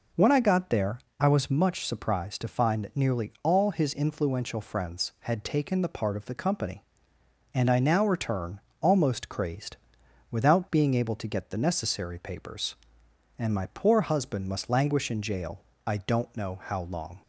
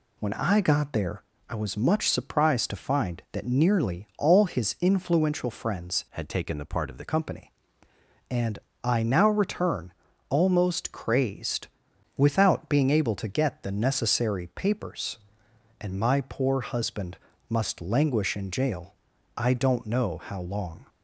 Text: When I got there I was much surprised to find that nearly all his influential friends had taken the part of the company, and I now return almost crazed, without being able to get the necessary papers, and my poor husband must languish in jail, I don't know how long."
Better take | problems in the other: first | pauses between "there" and "I"; slight; at 1.2 s; 0.26 s long; slight in the first // changes voice from "had" to "the"; from 6.0 to 7.0 s; 1.0 s long // pauses between "and" and "I"; slight; at 8.5 s; 0.24 s long // pauses between "return" and "almost"; slight; at 9.9 s; 0.36 s long; slight in the first // pauses between "husband" and "must"; slight; at 17.1 s; 0.32 s long

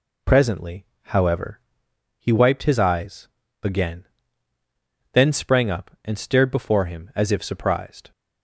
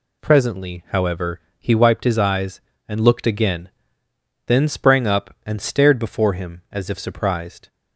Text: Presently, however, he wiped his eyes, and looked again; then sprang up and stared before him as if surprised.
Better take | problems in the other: second | skips "and looked"; at 3.4 s

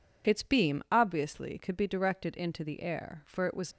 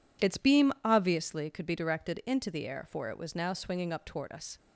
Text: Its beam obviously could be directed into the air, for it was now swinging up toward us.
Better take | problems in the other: second | stops before "now swinging up toward us"; at 3.7 s

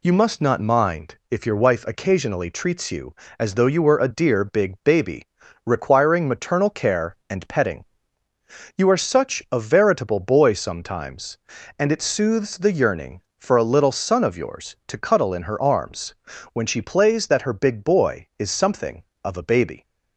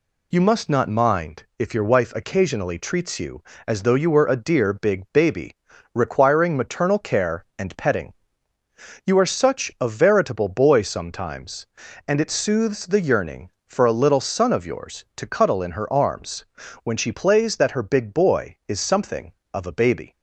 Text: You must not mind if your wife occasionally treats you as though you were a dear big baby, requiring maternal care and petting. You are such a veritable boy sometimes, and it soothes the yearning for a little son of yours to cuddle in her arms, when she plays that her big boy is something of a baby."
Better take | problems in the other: neither | none

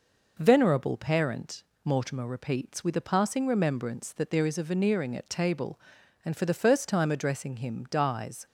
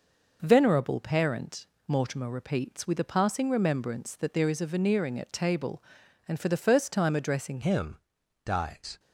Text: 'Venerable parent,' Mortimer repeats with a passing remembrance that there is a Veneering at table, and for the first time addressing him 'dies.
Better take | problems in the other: first | changes voice at "him"; from 7.6 s on; 1.3 s long // pauses between "him" and "dies"; noticeable; at 7.9 s; 0.48 s long

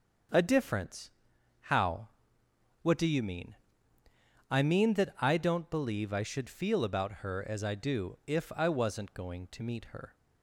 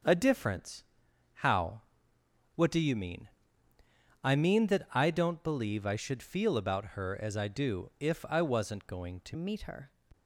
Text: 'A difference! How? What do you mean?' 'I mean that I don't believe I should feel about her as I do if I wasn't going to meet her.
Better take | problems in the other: first | starts louder than the rest; until 1.5 s; 7 dB; also in the first // changes voice at "meet"; from 9.3 s on; 0.6 s long

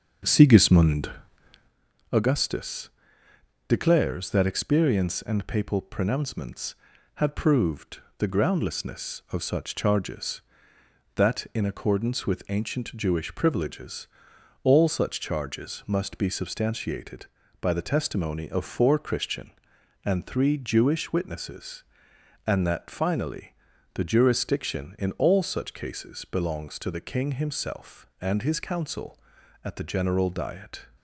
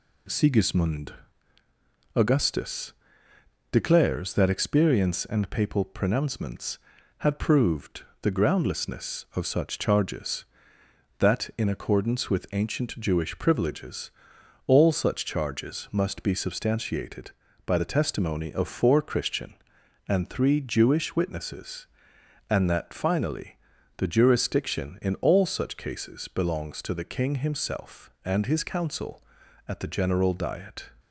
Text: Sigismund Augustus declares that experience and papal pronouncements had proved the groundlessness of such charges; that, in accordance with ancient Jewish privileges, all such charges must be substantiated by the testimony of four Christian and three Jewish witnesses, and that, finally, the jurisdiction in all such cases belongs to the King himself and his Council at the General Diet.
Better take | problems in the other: second | starts louder than the rest; until 1.8 s; 7 dB // pauses between "Sigismund" and "Augustus"; at 1.0 s; 1.0 s long; also in the second // pauses between "Augustus" and "declares"; noticeable; at 2.8 s; 0.80 s long; noticeable in the second // pauses between "proved" and "the"; slight; at 7.9 s; 0.20 s long; slight in the second

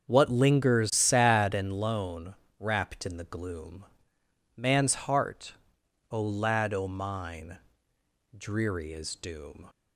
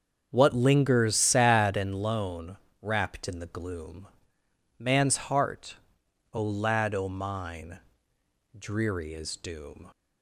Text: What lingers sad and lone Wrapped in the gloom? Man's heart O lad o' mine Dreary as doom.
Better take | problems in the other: neither | starts louder than the rest; the same in both // pauses between "lone" and "Wrapped"; slight; the same in both // pauses between "heart" and "O"; noticeable; the same in both // pauses between "mine" and "Dreary"; noticeable; the same in both

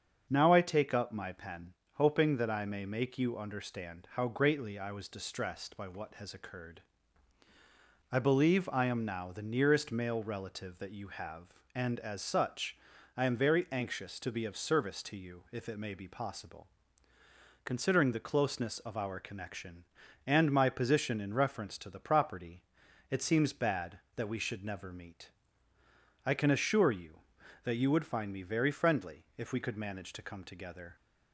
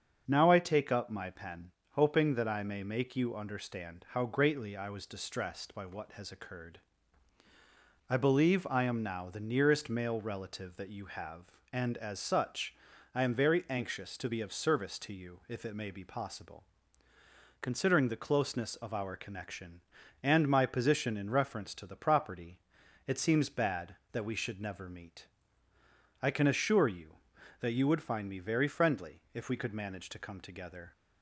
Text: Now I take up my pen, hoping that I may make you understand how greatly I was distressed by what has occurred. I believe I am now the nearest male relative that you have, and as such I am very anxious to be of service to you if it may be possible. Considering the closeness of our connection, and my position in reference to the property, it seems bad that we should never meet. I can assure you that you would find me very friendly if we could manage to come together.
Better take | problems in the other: neither | starts louder than the rest; the same in both // pauses between "such" and "I"; the same in both

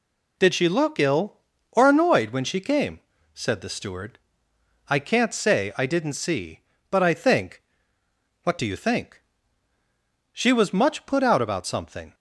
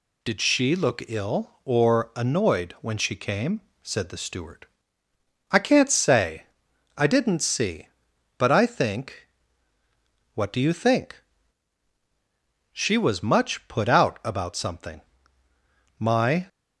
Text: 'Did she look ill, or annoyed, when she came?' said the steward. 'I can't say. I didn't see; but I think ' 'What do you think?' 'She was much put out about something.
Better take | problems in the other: first | goes on to say "My"; from 15.9 s on; 0.50 s long

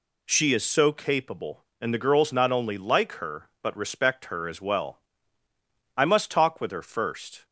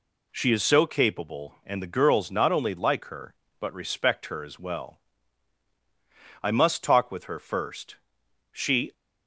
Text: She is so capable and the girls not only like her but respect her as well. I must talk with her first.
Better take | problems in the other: first | goes on to say "She"; slight; from 8.5 s on; 0.42 s long

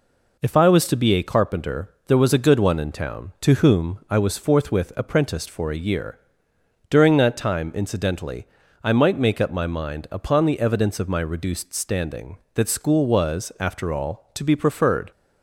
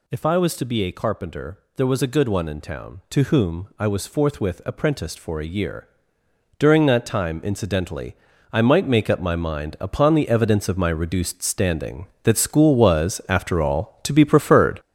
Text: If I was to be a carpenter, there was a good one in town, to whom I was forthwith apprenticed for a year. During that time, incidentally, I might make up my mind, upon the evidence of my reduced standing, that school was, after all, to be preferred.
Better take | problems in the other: first | gets louder; strong; throughout; 7 dB

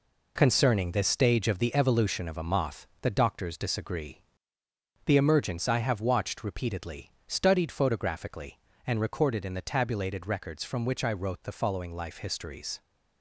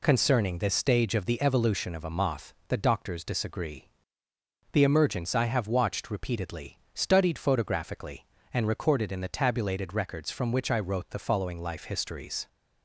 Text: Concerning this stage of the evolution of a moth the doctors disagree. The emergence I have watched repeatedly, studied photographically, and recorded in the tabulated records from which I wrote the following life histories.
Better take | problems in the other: second | gets quieter; strong; throughout; 7.5 dB

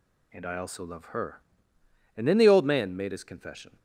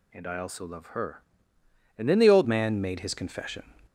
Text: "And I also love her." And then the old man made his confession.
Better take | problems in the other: first | changes voice at "man"; from 2.4 s on; 1.2 s long

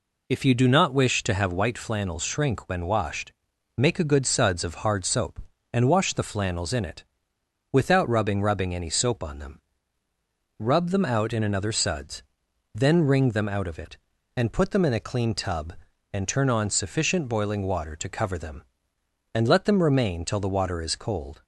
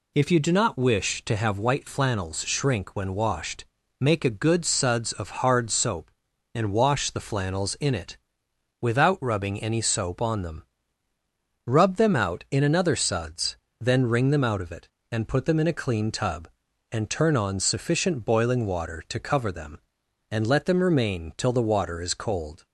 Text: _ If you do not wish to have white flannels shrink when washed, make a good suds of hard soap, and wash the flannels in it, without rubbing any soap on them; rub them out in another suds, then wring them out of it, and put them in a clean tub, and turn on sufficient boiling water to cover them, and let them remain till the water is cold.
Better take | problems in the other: second | says "rubbing" twice; at 8.4 s

